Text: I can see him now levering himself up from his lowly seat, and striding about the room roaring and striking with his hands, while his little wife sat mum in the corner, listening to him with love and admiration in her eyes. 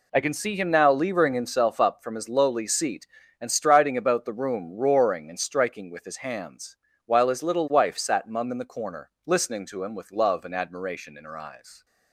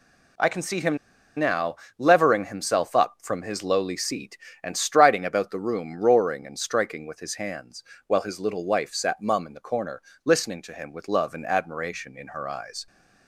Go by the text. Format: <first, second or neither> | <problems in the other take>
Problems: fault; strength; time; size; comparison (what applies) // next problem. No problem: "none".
first | pauses between "him" and "now"; at 0.9 s; 0.40 s long // pauses between "now" and "levering"; slight; at 1.7 s; 0.22 s long